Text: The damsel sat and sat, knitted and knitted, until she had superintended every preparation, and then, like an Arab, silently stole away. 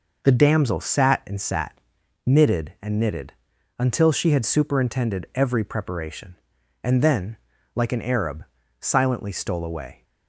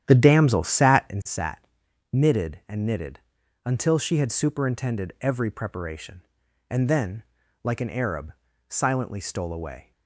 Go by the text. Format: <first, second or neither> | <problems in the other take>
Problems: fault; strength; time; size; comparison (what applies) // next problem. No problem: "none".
first | starts louder than the rest; strong; until 1.3 s; 10.5 dB